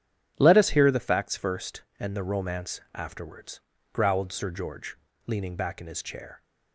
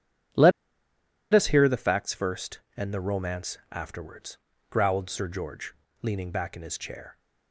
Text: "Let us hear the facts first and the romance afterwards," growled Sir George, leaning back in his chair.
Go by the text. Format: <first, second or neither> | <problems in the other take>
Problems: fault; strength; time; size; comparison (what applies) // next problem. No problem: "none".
first | starts louder than the rest; strong; until 2.1 s; 9 dB; strong in the first // pauses between "Let" and "us"; noticeable; at 0.5 s; 0.82 s long